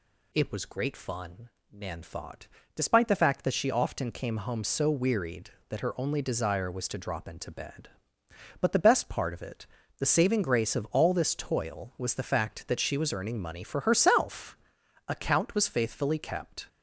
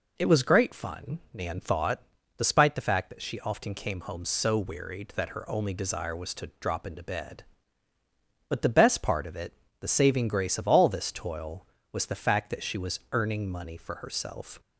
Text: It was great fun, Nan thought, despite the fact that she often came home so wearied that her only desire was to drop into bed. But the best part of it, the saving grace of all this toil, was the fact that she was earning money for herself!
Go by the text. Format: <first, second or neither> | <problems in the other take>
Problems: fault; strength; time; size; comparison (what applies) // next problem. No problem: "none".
second | goes on to say "Account was faithfully kept"; from 15.0 s on; 1.5 s long